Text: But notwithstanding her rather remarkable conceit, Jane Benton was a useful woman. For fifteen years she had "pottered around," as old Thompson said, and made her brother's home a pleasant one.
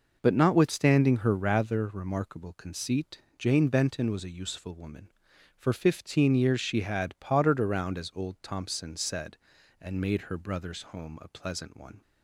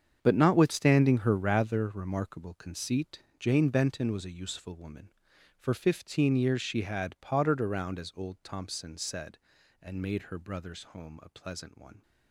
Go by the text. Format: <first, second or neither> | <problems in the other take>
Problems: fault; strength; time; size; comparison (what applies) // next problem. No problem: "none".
first | gets quieter; strong; throughout; 13.5 dB